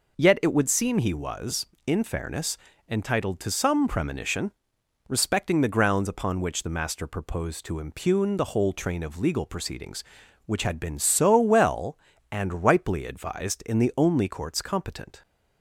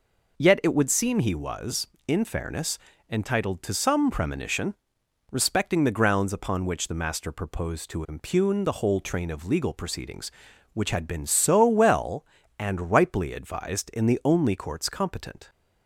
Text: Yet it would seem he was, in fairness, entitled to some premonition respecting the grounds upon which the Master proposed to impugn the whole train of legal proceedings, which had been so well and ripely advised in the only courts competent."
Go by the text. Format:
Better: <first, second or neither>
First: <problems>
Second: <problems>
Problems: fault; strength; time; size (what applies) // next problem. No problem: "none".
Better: neither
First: pauses between "premonition" and "respecting"; noticeable; at 4.5 s; 0.58 s long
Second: pauses between "premonition" and "respecting"; noticeable; at 4.7 s; 0.58 s long